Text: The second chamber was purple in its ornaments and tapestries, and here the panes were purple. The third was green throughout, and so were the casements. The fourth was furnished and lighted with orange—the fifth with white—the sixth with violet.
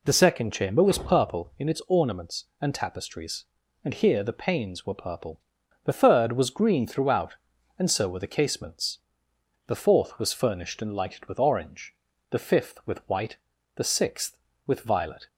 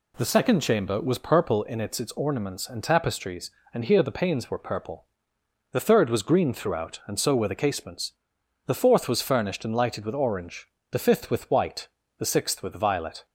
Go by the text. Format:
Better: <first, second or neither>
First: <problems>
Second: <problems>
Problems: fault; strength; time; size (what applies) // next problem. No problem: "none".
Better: first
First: none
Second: says "its" twice; at 1.9 s